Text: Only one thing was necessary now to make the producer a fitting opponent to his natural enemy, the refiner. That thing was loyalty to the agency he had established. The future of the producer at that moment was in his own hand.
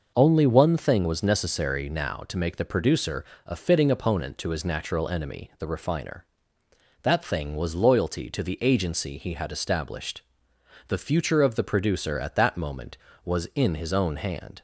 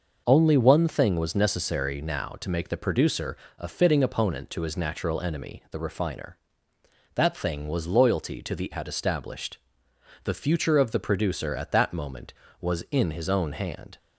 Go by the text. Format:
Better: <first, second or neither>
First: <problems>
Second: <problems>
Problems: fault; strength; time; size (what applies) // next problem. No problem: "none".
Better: first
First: pauses between "producer" and "a"; slight; at 3.2 s; 0.22 s long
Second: pauses between "producer" and "a"; slight; at 3.3 s; 0.22 s long // skips "agency he"; at 8.7 s